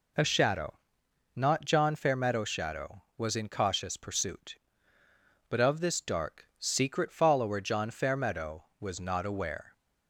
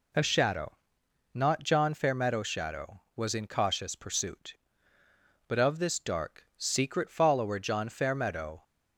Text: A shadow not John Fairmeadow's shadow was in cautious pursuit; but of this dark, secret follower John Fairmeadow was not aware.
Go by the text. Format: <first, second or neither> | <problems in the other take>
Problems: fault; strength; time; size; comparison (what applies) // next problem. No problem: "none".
first | pauses between "shadow" and "not"; noticeable; at 0.7 s; 0.56 s long; noticeable in the first // stops before "was not aware"; at 8.6 s